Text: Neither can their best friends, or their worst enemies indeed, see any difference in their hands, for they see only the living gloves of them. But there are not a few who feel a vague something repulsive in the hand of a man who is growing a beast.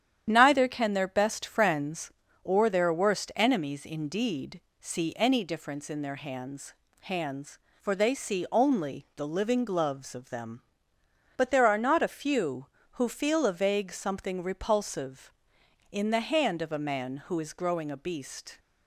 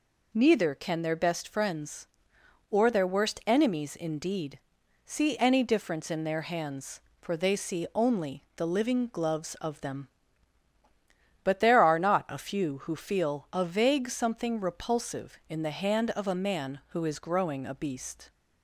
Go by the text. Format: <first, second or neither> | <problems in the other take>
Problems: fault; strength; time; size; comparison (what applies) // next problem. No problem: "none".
second | starts louder than the rest; strong; until 1.2 s; 10 dB // says "hands" twice; at 6.9 s